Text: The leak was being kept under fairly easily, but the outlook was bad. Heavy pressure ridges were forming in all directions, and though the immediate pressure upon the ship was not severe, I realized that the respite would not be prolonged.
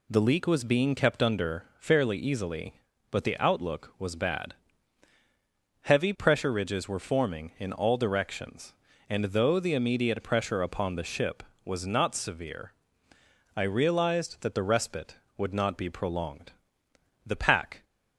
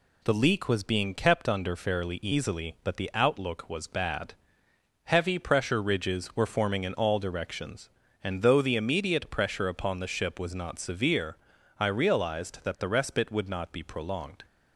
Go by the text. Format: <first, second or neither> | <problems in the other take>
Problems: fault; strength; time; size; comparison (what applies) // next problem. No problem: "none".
second | goes on to say "The pack"; from 17.2 s on; 0.60 s long